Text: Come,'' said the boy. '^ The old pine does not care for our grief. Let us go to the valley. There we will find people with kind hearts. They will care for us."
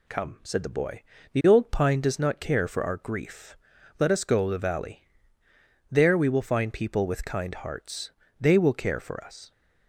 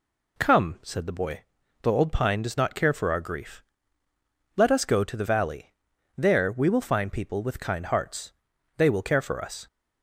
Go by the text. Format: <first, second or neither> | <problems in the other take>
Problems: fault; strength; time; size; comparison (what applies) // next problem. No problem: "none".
second | skips "to"; at 4.4 s